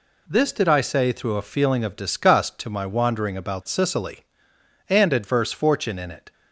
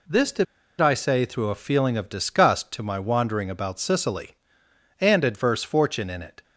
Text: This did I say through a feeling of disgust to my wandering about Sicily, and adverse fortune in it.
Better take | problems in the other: first | pauses between "did" and "I"; slight; at 0.4 s; 0.35 s long

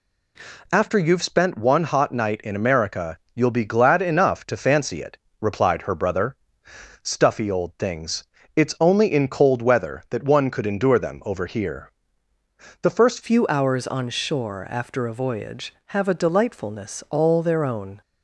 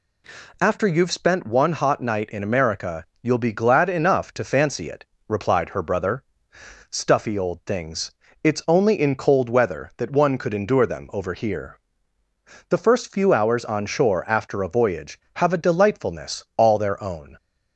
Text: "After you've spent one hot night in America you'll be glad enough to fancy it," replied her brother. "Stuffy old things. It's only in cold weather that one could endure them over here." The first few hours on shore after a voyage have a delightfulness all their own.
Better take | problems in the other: second | pauses between "America" and "you'll"; slight; at 3.1 s; 0.16 s long; slight in the second // changes voice at "few"; from 13.2 s on; 4.8 s long

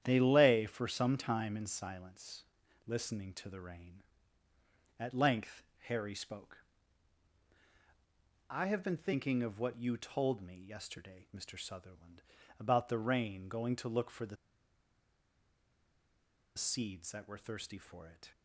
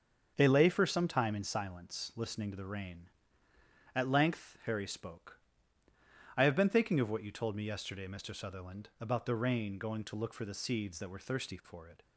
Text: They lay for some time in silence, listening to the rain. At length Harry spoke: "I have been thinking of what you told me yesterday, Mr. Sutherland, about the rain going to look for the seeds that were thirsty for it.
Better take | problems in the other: second | starts louder than the rest; strong; until 1.0 s; 10 dB; also in the second // pauses between "length" and "Harry"; slight; at 5.6 s; 0.24 s long // pauses between "the" and "seeds"; strong; at 14.3 s; 2.2 s long

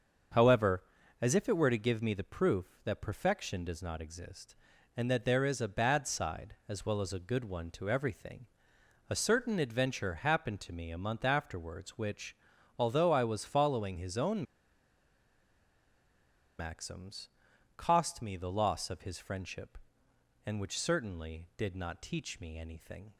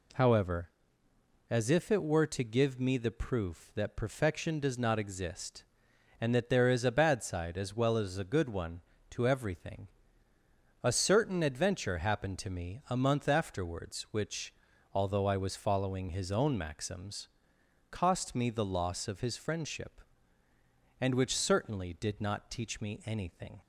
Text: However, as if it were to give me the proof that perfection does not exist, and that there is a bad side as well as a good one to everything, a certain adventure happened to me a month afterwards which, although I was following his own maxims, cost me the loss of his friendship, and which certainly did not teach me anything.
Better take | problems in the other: second | starts louder than the rest; until 1.7 s; 7 dB // pauses between "own" and "maxims"; strong; at 14.4 s; 2.1 s long

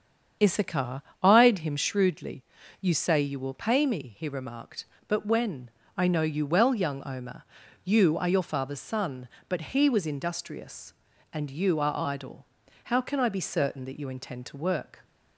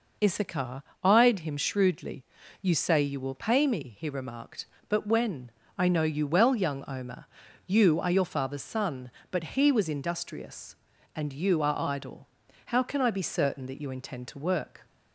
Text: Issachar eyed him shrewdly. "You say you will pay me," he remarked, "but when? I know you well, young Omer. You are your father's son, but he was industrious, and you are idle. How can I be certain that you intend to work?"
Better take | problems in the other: second | starts louder than the rest; strong; until 2.0 s; 7.5 dB // pauses between "Issachar" and "eyed"; slight; at 0.9 s; 0.22 s long; slight in the second

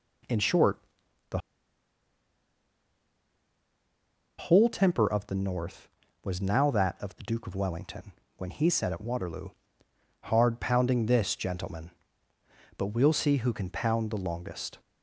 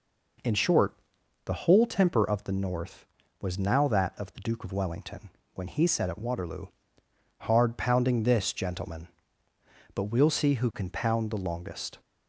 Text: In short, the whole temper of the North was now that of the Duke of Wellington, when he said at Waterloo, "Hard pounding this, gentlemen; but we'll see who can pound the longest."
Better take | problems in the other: second | pauses between "the" and "whole"; strong; at 1.3 s; 3.0 s long

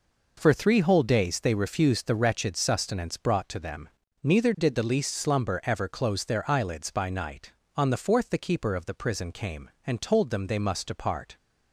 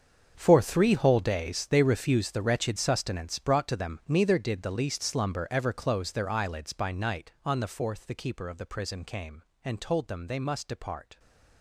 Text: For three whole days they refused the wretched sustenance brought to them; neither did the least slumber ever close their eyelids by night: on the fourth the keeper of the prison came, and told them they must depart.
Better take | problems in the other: first | gets quieter; strong; throughout; 15 dB

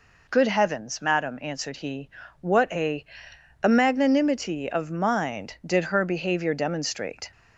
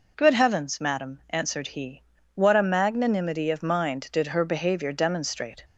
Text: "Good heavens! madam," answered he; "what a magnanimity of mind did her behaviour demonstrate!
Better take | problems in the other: second | says "a" twice; at 3.6 s

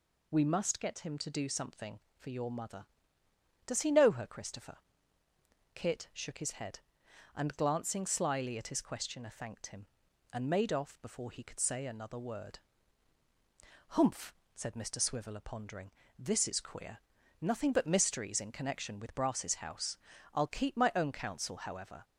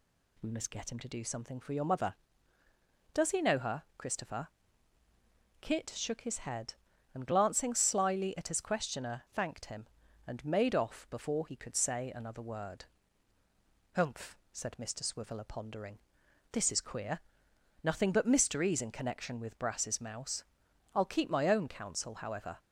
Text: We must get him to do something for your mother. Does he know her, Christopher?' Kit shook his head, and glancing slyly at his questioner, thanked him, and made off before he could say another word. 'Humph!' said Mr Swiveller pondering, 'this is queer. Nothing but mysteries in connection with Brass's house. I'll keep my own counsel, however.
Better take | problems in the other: first | says "mouse" for "house"; at 19.9 s

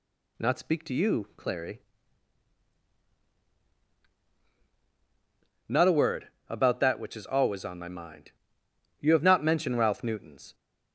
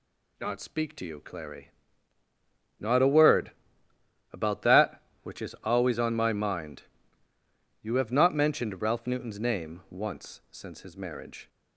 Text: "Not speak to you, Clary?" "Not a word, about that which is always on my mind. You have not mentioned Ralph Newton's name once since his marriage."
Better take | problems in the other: second | stops before "name once since his marriage"; at 10.5 s

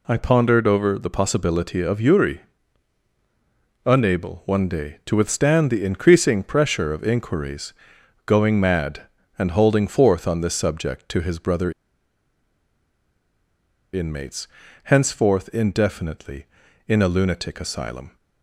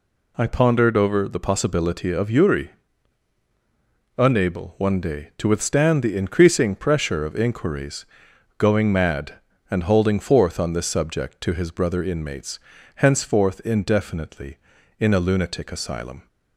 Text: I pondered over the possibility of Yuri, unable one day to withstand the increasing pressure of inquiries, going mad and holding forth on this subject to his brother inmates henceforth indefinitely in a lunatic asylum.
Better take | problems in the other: second | pauses between "brother" and "inmates"; strong; at 11.7 s; 2.2 s long // pauses between "inmates" and "henceforth"; at 14.4 s; 0.38 s long; also in the second

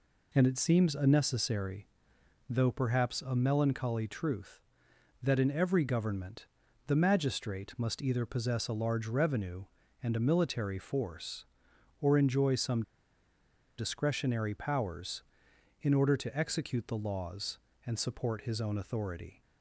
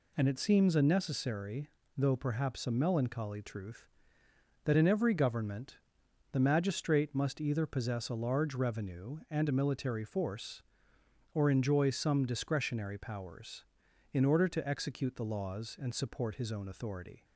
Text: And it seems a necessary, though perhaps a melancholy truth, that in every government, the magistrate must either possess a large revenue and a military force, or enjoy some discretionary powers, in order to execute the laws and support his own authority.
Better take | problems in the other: second | pauses between "some" and "discretionary"; noticeable; at 12.8 s; 0.96 s long

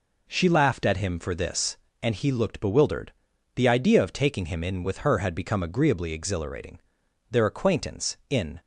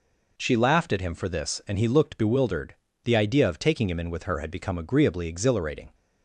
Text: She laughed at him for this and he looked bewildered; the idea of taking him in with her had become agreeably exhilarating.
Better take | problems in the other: second | goes on to say "Their acquaintance in"; noticeable; from 7.3 s on; 1.2 s long

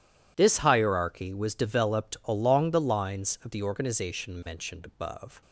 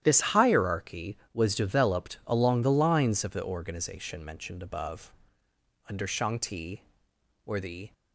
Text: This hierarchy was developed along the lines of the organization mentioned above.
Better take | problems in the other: first | starts louder than the rest; strong; until 1.0 s; 11 dB // goes on to say "Under Shang Ti were the"; strong; from 5.8 s on; 2.0 s long

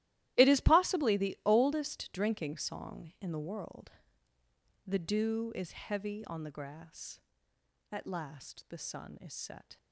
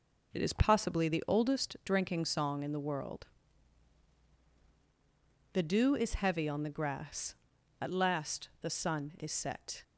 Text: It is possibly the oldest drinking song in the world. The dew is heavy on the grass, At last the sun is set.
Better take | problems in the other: second | gets quieter; strong; throughout; 16 dB

